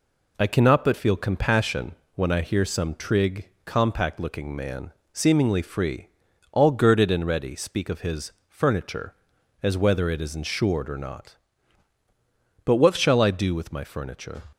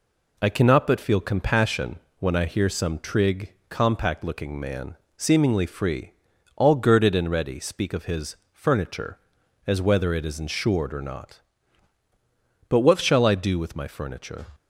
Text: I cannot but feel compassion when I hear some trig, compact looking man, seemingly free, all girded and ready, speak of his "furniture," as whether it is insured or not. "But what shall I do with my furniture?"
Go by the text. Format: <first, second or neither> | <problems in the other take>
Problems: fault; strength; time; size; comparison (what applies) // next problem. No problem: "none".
neither | pauses between "compassion" and "when"; slight; the same in both // pauses between "his" and "furniture"; slight; the same in both